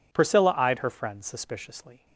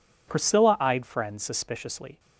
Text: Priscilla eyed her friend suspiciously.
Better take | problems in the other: first | skips "her"; at 1.0 s

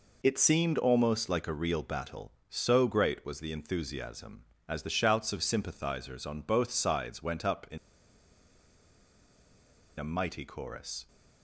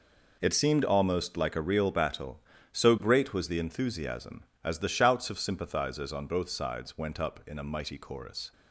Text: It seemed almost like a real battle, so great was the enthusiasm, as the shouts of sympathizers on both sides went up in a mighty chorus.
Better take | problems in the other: second | pauses between "in" and "a"; strong; at 7.7 s; 2.1 s long

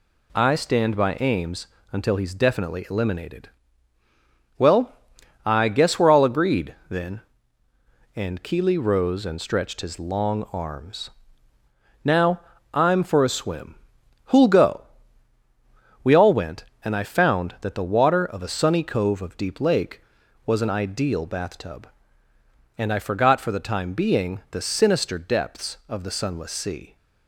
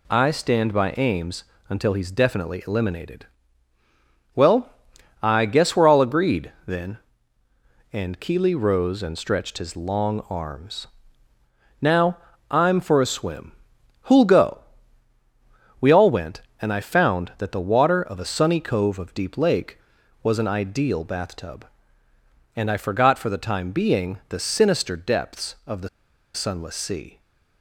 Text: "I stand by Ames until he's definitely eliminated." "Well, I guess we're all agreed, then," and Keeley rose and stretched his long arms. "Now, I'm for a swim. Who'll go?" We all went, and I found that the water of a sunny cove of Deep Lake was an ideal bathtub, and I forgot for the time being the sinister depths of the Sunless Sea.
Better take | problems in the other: first | pauses between "Ames" and "until"; slight; at 1.4 s; 0.24 s long; slight in the first // pauses between "the" and "Sunless"; noticeable; at 25.8 s; 0.46 s long

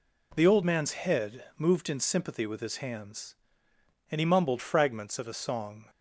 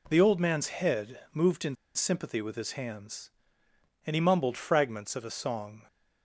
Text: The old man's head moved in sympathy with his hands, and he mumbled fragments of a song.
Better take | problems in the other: first | pauses between "head" and "moved"; slight; at 1.1 s; 0.16 s long; slight in the first // pauses between "in" and "sympathy"; slight; at 1.7 s; 0.20 s long

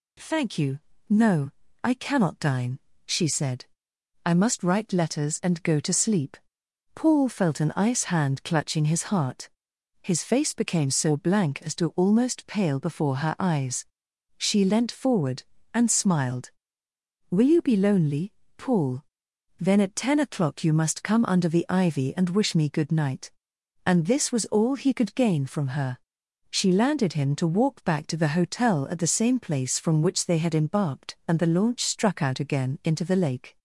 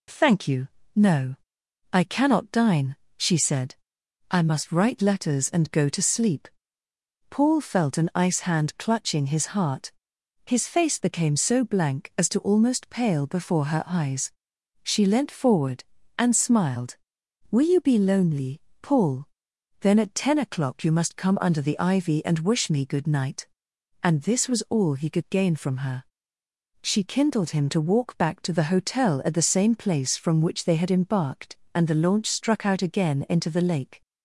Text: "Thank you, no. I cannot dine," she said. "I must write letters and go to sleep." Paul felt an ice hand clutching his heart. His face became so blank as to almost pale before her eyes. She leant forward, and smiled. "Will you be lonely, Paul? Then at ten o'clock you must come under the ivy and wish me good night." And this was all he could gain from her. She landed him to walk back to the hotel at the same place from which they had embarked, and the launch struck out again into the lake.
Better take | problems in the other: first | says "kindled" for "landed"; at 27.0 s

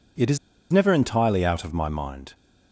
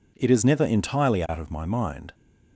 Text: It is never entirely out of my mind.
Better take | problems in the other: second | pauses between "is" and "never"; slight; at 0.3 s; 0.35 s long

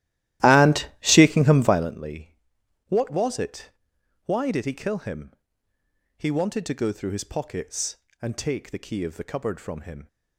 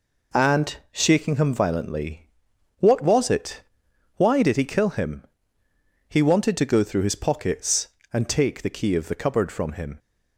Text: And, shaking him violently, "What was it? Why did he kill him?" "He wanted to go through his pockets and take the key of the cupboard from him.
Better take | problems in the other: second | starts louder than the rest; strong; until 2.0 s; 14.5 dB

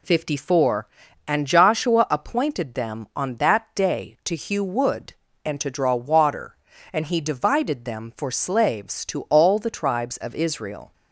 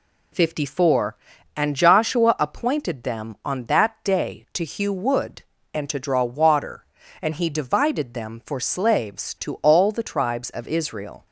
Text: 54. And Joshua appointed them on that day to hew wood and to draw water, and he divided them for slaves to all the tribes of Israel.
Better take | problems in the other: neither | none

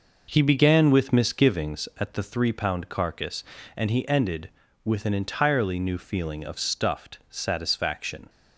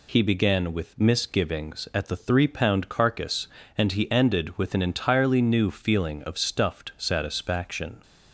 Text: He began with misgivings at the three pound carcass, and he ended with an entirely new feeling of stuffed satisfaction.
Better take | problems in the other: second | starts louder than the rest; noticeable; until 1.9 s; 5.5 dB

